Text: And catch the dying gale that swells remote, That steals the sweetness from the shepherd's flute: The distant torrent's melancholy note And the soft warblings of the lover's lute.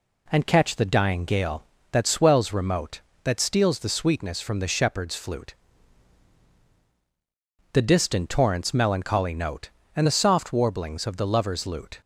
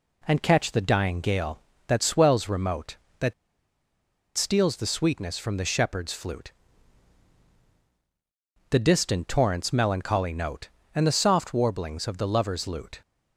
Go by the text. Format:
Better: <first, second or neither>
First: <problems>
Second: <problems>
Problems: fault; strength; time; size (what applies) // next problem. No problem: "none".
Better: first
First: none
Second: pauses between "That" and "steals"; at 3.3 s; 1.0 s long